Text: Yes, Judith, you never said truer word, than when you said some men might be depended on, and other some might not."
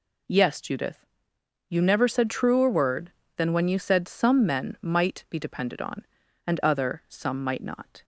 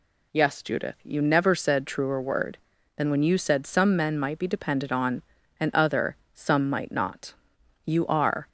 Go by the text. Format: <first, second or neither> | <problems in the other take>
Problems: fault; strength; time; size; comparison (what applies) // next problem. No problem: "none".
first | pauses between "other" and "some"; slight; at 6.1 s; 0.18 s long // goes on to say "You are"; noticeable; from 7.8 s on; 0.64 s long